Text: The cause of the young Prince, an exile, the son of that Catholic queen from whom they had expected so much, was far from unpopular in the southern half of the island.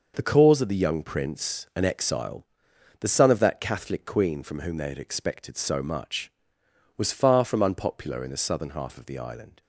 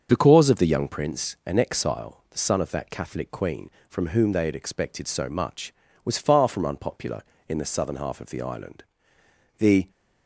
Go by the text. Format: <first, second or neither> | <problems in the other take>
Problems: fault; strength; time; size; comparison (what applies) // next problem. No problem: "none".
first | starts louder than the rest; until 1.1 s; 6.5 dB // goes on to say "The"; slight; from 9.5 s on; 0.32 s long